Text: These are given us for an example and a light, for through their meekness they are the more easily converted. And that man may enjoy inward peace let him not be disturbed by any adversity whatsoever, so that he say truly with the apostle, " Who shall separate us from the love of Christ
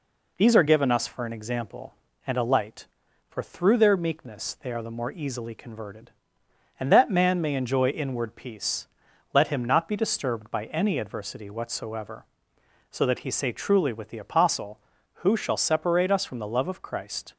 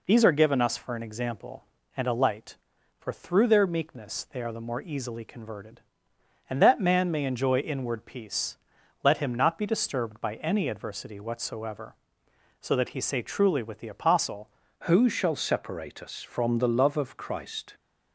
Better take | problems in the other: first | pauses between "peace" and "let"; noticeable; at 8.5 s; 0.46 s long; noticeable in the first // changes voice at "Who"; from 14.8 s on; 2.9 s long

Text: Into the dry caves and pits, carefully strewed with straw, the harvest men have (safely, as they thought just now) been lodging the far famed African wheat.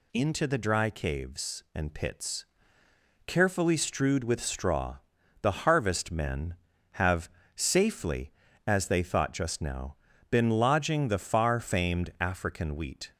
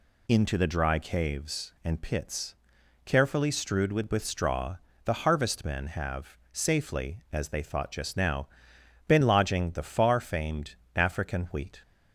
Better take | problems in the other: first | says "with" twice; at 4.0 s // pauses between "famed" and "African"; slight; at 10.7 s; 0.18 s long

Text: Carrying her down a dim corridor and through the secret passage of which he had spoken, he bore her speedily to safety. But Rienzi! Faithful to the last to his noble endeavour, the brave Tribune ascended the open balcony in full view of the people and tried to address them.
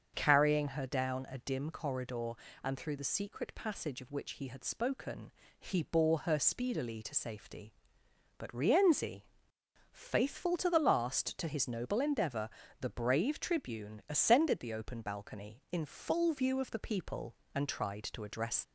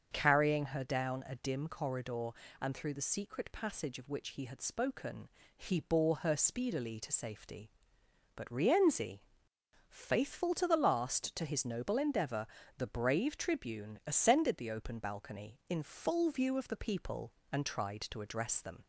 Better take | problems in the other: second | starts louder than the rest; until 1.1 s; 7 dB; also in the second // stops before "them"; at 18.6 s

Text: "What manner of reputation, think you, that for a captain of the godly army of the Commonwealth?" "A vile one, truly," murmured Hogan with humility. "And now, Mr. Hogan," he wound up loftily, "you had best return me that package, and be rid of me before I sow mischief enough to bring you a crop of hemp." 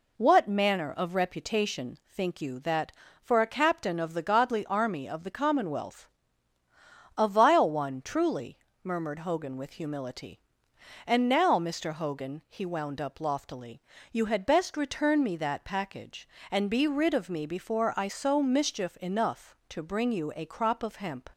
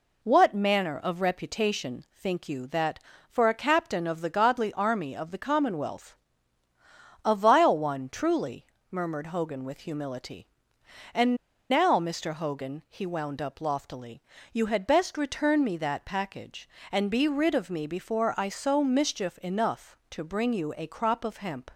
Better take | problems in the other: first | pauses between "And" and "now"; slight; at 11.3 s; 0.36 s long

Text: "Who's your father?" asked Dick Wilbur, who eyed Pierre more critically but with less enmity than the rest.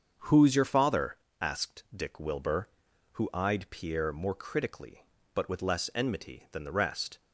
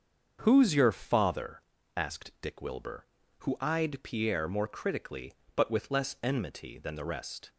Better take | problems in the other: neither | starts louder than the rest; the same in both

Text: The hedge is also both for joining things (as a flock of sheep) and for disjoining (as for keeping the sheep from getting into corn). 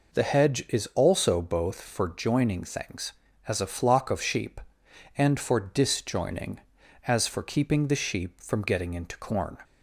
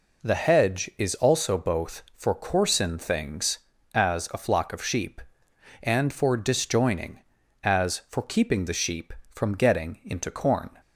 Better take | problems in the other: first | says "coarsen" for "joining"; at 2.3 s

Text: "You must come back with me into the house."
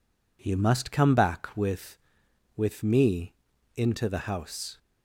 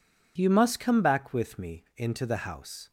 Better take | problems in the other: second | says "with" twice; at 2.5 s // pauses between "me" and "into"; at 3.3 s; 0.42 s long

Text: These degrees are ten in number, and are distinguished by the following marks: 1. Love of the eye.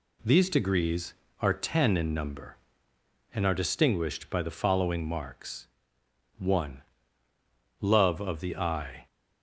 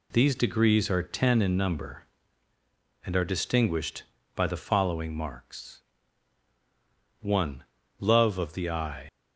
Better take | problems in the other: first | leaves "eye" unfinished; at 9.0 s; 80 ms

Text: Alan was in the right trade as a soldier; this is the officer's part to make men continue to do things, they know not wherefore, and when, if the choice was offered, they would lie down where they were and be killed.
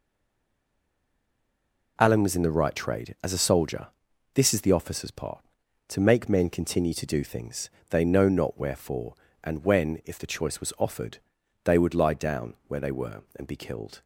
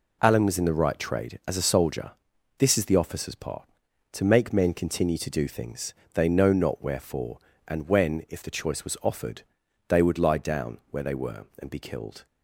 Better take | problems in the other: second | stays silent before the first word; noticeable; until 1.9 s; 1.9 s long // pauses between "down" and "where"; slight; at 12.5 s; 0.16 s long

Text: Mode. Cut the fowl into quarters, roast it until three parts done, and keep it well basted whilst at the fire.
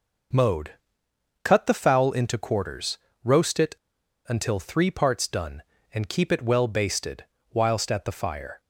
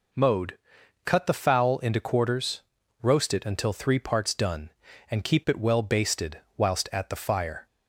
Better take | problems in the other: second | pauses between "it" and "until"; noticeable; at 3.7 s; 0.52 s long // pauses between "basted" and "whilst"; slight; at 7.2 s; 0.28 s long; slight in the second

